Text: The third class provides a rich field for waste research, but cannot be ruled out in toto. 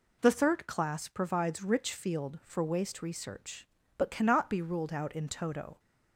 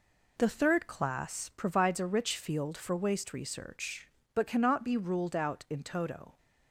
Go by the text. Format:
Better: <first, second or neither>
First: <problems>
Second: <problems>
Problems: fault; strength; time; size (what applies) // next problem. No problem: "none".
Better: second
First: skips "a"; at 1.6 s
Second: none